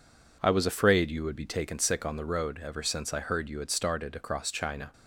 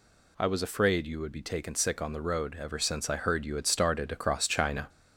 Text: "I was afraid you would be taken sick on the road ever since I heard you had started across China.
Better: first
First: none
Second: gets louder; slight; throughout; 3 dB

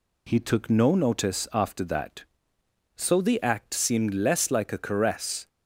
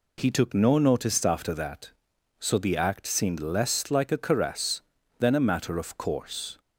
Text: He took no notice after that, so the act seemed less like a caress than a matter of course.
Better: second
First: stops before "than a matter of course"; at 5.4 s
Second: none

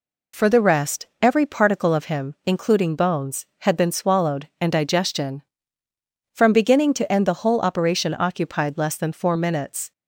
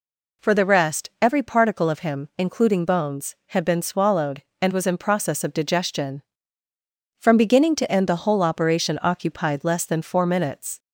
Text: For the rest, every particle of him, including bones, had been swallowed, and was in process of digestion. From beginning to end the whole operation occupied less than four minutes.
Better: second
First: skips "was in process of"; at 4.7 s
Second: none

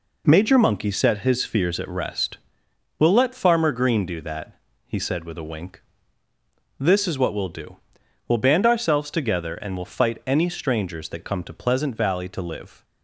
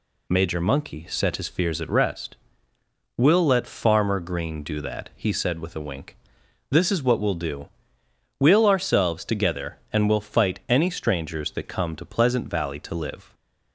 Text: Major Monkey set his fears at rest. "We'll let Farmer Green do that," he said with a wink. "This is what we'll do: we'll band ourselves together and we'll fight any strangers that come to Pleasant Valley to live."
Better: first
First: none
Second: skips "band"; at 8.6 s

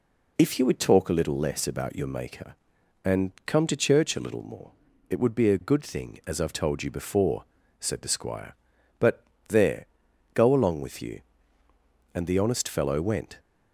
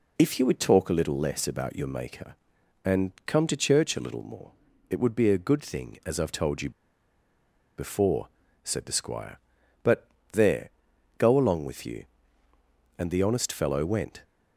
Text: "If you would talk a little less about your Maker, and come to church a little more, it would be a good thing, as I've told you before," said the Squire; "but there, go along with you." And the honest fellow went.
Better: first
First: pauses between "but" and "there"; slight; at 9.2 s; 0.24 s long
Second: pauses between "you" and "before"; at 6.6 s; 1.0 s long // pauses between "but" and "there"; slight; at 10.0 s; 0.24 s long

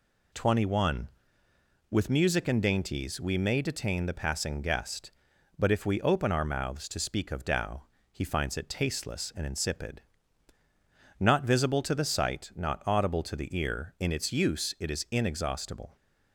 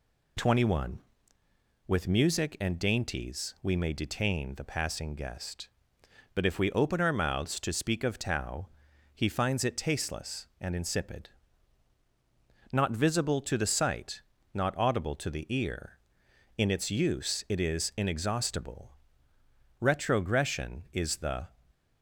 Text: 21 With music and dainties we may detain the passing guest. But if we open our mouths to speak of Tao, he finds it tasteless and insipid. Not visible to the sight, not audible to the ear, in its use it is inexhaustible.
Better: first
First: none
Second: goes on to say "Retrogression is the"; strong; from 19.7 s on; 1.6 s long

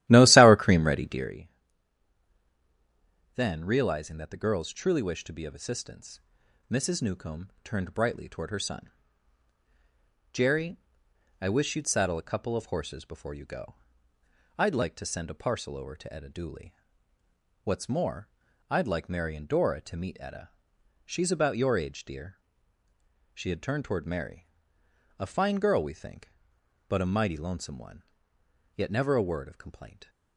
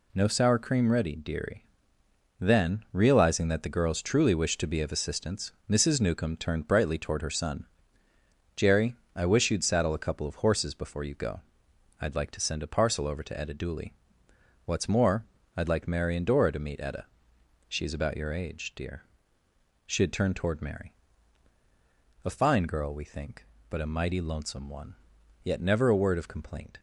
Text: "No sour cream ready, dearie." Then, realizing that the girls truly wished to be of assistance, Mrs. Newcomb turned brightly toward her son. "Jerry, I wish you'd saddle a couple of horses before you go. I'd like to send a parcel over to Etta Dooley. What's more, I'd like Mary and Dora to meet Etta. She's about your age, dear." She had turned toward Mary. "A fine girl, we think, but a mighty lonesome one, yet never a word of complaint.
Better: second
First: starts louder than the rest; strong; until 1.4 s; 14.5 dB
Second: none

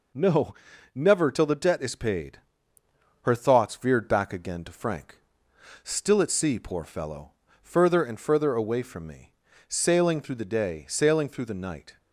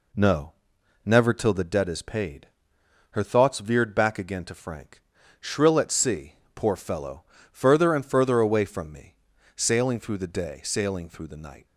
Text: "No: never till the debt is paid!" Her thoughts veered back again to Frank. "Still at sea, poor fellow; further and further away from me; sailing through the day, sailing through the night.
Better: first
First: none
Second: says "Shrill" for "Still"; at 5.3 s

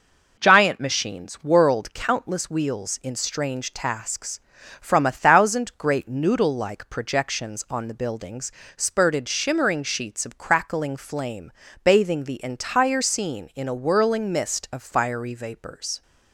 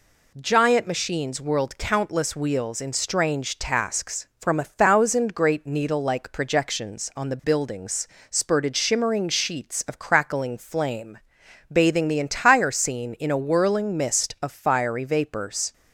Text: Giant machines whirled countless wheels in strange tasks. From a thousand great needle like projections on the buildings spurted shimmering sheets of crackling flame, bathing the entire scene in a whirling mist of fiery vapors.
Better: second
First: says "noodle" for "needle"; at 6.0 s // pauses between "buildings" and "spurted"; slight; at 8.5 s; 0.24 s long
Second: pauses between "buildings" and "spurted"; slight; at 8.0 s; 0.22 s long

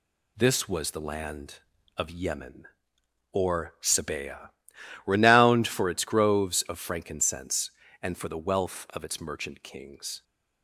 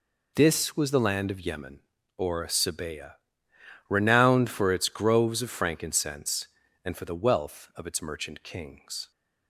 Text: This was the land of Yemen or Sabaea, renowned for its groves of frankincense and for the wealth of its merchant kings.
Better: neither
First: none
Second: none

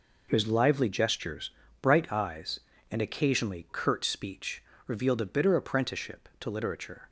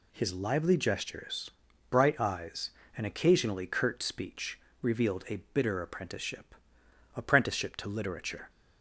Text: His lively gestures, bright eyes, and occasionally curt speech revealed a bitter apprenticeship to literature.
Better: first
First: pauses between "speech" and "revealed"; slight; at 4.6 s; 0.22 s long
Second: pauses between "speech" and "revealed"; slight; at 4.5 s; 0.22 s long // pauses between "a" and "bitter"; slight; at 5.3 s; 0.16 s long // says "apprenticeship" twice; at 7.1 s

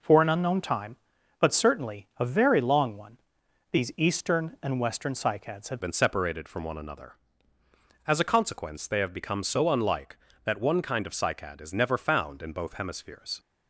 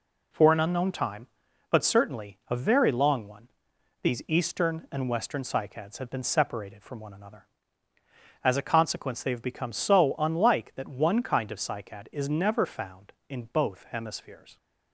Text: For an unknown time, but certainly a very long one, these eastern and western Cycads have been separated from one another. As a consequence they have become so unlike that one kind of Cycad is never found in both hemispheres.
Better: second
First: changes voice at "been"; from 5.8 s on; 7.5 s long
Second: none

